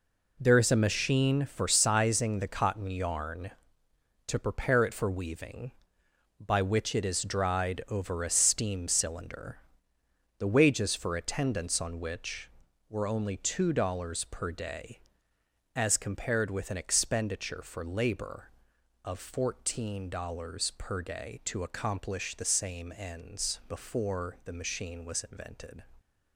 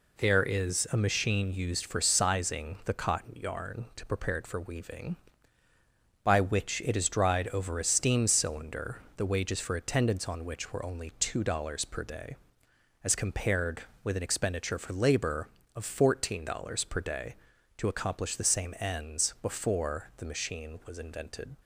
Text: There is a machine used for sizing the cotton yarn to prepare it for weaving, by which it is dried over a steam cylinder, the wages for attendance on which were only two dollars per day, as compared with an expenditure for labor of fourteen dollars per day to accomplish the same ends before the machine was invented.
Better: second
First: skips "used"; at 1.4 s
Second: none

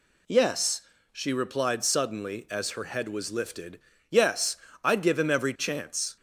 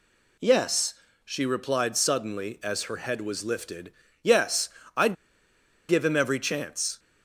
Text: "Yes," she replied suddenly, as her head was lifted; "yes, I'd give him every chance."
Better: first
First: none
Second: pauses between "I'd" and "give"; noticeable; at 5.1 s; 0.73 s long

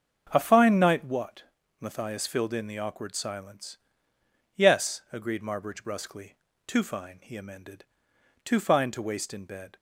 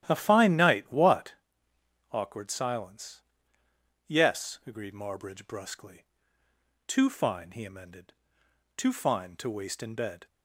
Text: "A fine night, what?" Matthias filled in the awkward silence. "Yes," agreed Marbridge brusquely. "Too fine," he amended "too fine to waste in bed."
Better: first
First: starts louder than the rest; until 1.3 s; 7 dB // pauses between "amended" and "too"; noticeable; at 7.8 s; 0.58 s long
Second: starts louder than the rest; strong; until 1.0 s; 11.5 dB // skips "Matthias filled in the"; at 1.7 s // pauses between "amended" and "too"; noticeable; at 8.1 s; 0.64 s long

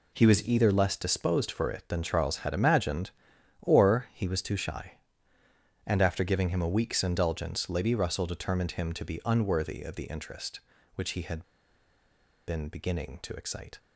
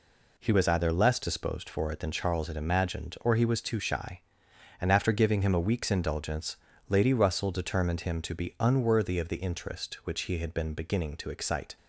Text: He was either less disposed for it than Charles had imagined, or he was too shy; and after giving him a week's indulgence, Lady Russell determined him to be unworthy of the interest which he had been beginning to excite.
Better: second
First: pauses between "had" and "been"; at 11.4 s; 1.0 s long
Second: none

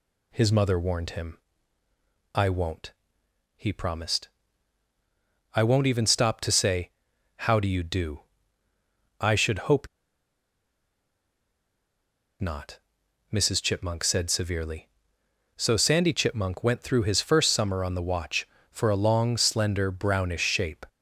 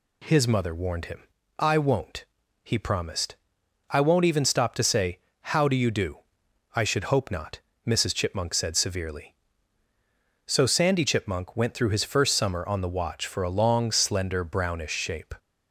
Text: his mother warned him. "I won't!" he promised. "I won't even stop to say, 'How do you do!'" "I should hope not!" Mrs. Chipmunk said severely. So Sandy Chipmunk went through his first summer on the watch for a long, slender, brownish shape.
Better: second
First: pauses between "hope" and "not"; strong; at 9.8 s; 2.5 s long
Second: none

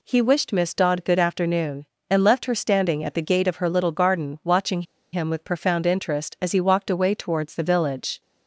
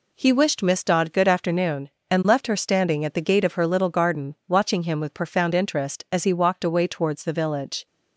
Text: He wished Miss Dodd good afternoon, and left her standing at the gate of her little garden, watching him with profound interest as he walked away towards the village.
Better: second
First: pauses between "watching" and "him"; slight; at 4.8 s; 0.30 s long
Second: none

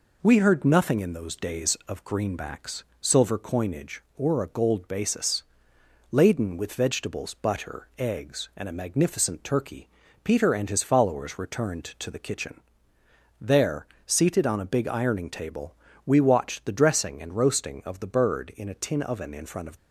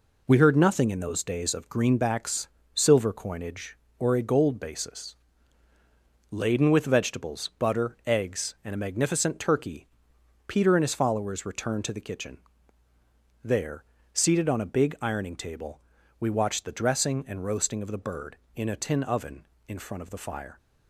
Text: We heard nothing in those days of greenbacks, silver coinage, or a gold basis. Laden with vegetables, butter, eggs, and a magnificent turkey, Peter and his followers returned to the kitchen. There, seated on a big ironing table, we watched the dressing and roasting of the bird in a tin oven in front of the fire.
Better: second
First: stops before "the fire"; at 19.7 s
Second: none

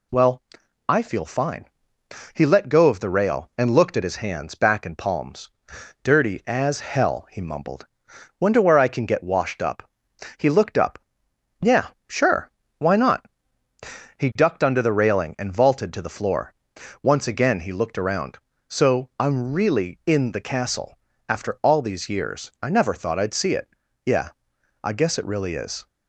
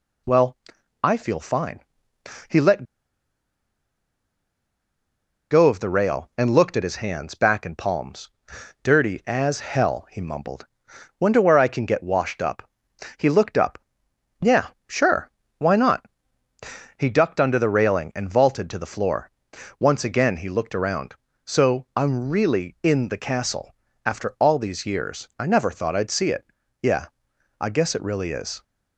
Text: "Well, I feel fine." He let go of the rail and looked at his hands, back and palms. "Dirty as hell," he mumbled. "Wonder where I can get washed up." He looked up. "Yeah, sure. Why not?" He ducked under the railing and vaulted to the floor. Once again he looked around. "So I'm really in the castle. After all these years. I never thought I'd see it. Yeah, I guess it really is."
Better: first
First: none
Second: pauses between "let" and "go"; strong; at 2.8 s; 2.6 s long

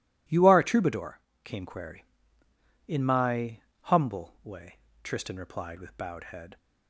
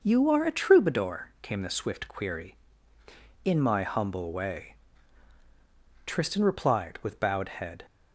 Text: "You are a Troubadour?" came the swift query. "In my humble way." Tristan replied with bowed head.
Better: second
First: skips "the swift"; at 1.6 s // pauses between "my" and "humble"; slight; at 3.6 s; 0.22 s long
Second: none

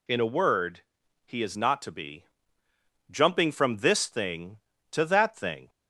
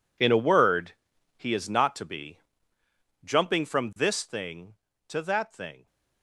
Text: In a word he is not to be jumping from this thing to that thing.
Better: first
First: pauses between "word" and "he"; at 0.8 s; 0.44 s long // pauses between "be" and "jumping"; noticeable; at 2.2 s; 0.84 s long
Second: gets quieter; strong; throughout; 15.5 dB // pauses between "word" and "he"; at 0.9 s; 0.44 s long // pauses between "be" and "jumping"; noticeable; at 2.3 s; 0.84 s long

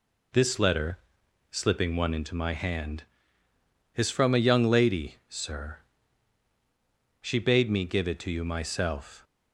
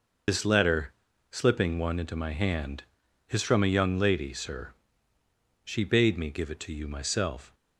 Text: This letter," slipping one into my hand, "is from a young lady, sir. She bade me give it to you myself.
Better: first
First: none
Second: loses the start of "This"; at 0.2 s; 60 ms

